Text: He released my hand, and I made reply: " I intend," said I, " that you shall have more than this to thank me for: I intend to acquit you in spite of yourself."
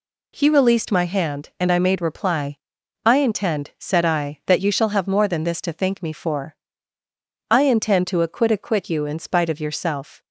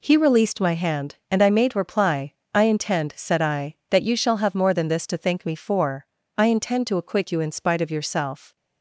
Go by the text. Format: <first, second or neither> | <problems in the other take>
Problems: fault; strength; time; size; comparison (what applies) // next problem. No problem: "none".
second | says "acquit" twice; at 8.5 s